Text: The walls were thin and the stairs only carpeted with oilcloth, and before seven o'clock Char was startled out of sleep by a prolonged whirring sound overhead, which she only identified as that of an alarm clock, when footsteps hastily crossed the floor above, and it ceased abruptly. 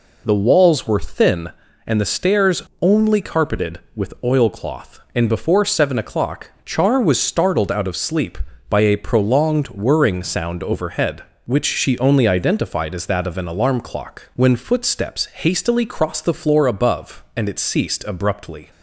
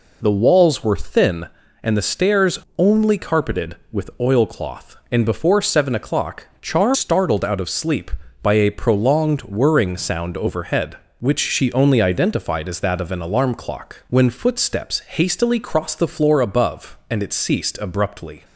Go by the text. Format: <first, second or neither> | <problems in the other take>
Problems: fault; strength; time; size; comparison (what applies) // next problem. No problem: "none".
first | pauses between "stairs" and "only"; slight; at 2.5 s; 0.18 s long; slight in the first // pauses between "o'clock" and "Char"; slight; at 6.4 s; 0.16 s long; slight in the first // skips "was"; at 6.9 s